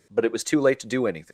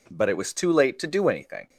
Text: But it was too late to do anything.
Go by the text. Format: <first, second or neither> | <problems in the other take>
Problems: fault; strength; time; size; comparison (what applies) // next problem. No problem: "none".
second | leaves "anything" unfinished; at 1.2 s; 90 ms